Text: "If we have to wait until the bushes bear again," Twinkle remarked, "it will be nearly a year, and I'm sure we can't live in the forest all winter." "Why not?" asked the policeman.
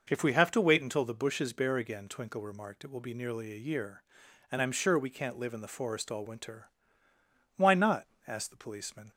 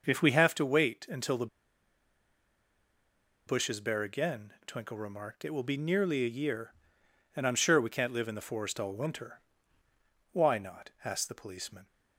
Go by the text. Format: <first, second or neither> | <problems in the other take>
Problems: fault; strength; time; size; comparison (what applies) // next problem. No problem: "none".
first | pauses between "the" and "bushes"; strong; at 1.4 s; 2.0 s long